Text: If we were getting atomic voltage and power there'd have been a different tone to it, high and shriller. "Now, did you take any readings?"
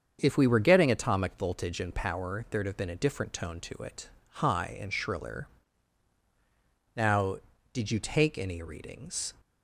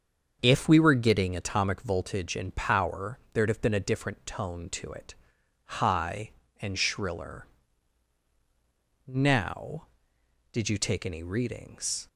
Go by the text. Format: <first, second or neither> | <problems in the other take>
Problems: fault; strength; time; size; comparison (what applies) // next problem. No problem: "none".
neither | starts louder than the rest; the same in both